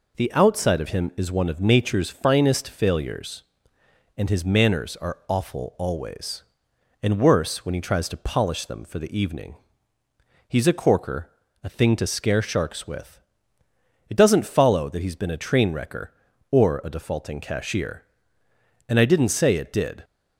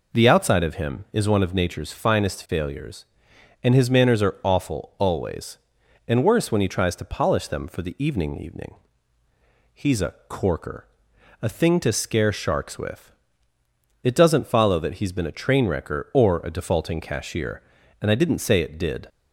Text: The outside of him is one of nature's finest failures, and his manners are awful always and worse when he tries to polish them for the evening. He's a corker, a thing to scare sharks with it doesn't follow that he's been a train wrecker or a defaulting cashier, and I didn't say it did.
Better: first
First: pauses between "with" and "it"; noticeable; at 13.1 s; 0.90 s long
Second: says "evening" twice; at 8.3 s // pauses between "with" and "it"; noticeable; at 13.1 s; 0.94 s long

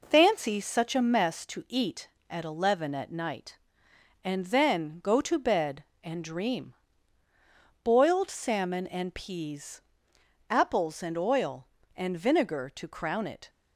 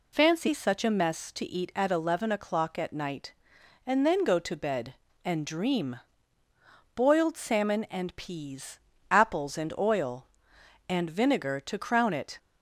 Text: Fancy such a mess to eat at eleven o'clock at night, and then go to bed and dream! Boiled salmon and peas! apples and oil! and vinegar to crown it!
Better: second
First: skips "o'clock"; at 2.9 s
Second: none

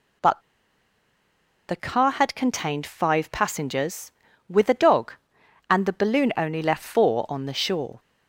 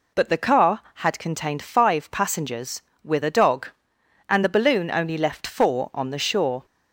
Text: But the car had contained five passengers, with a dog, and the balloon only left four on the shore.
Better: second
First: pauses between "But" and "the"; strong; at 0.4 s; 1.2 s long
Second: none

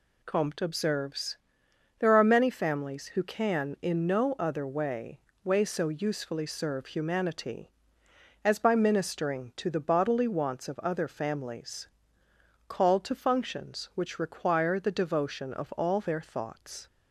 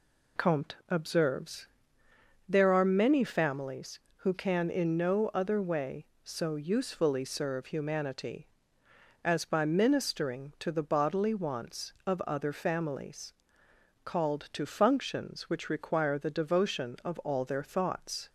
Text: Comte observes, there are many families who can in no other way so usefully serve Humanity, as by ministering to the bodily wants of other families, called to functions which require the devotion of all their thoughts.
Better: second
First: says "way" twice; at 5.4 s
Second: none

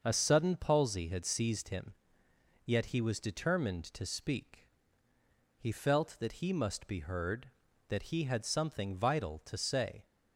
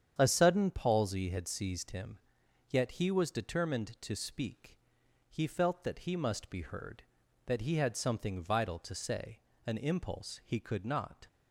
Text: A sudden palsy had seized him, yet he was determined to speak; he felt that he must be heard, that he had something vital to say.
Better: first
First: starts louder than the rest; until 1.0 s; 6.5 dB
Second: starts louder than the rest; strong; until 1.1 s; 8.5 dB // goes on to say "An impulse he could not"; from 9.6 s on; 1.6 s long

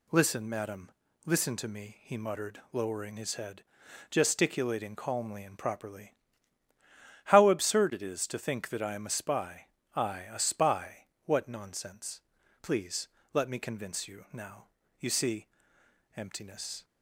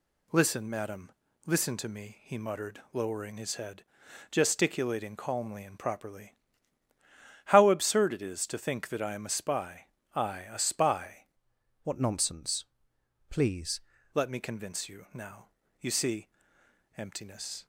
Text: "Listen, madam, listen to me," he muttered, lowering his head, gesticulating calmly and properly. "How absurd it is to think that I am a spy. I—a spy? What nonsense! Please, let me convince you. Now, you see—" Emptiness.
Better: first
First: none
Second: changes voice from "What" to "Please"; from 11.8 to 13.7 s; 1.9 s long

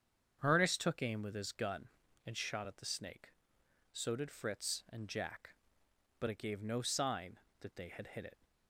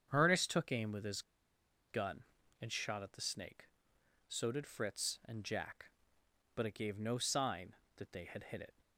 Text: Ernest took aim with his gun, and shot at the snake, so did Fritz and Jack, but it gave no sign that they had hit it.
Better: first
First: starts louder than the rest; strong; until 1.4 s; 7.5 dB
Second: starts louder than the rest; strong; until 1.1 s; 7.5 dB // pauses between "his" and "gun"; noticeable; at 1.2 s; 0.67 s long

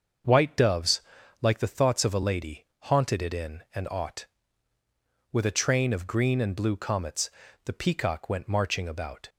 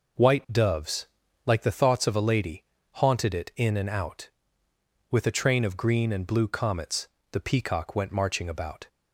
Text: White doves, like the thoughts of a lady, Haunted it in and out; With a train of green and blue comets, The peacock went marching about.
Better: second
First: starts louder than the rest; until 1.6 s; 6.5 dB // says "ought" for "out"; at 3.8 s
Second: none

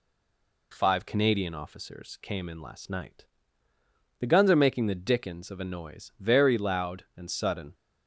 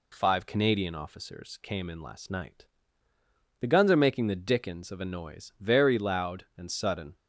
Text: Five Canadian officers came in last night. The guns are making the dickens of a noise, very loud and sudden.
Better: second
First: stays silent before the first word; slight; until 0.7 s; 0.7 s long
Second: none

